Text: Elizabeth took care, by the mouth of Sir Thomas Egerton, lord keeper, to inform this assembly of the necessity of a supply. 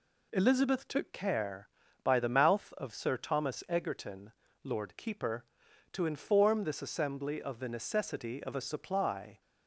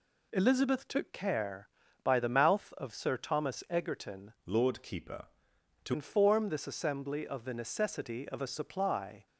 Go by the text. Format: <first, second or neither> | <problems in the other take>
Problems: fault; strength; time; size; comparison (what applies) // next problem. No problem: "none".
first | changes voice from "lord" to "to"; from 4.4 to 5.9 s; 1.5 s long